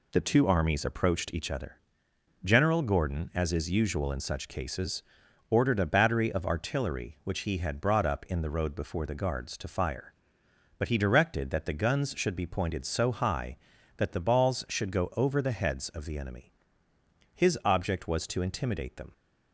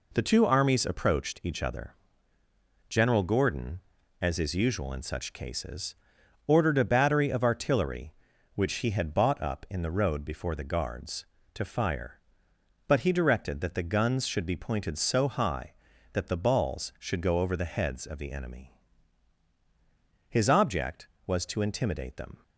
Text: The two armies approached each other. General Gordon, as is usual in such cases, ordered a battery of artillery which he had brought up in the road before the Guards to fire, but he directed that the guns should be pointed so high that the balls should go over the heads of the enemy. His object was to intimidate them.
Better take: first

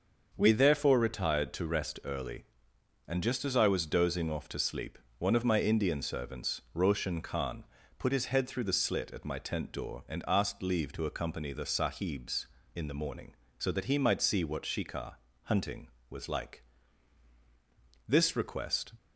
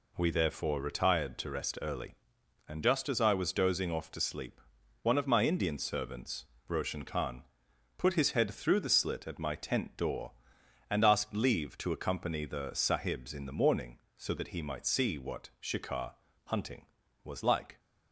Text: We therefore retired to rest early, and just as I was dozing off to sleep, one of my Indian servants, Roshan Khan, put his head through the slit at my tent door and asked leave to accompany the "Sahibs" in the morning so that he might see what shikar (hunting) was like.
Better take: second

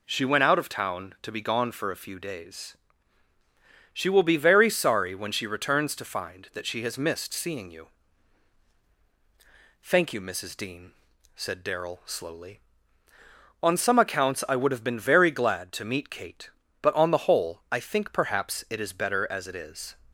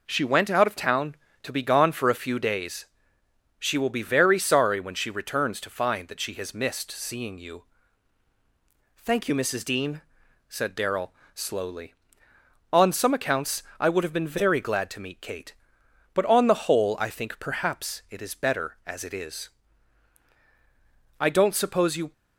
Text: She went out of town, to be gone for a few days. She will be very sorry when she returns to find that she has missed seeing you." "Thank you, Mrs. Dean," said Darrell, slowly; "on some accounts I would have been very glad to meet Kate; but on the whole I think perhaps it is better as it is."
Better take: first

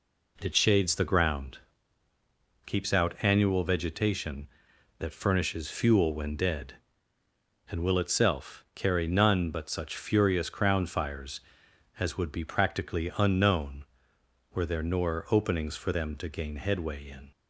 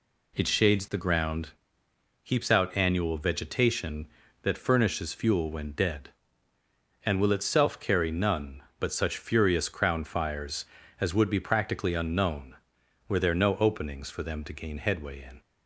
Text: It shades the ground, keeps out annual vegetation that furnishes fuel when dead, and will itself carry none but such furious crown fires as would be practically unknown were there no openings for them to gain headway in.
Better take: second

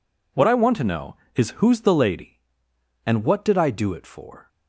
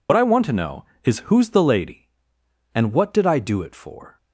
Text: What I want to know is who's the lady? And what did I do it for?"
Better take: first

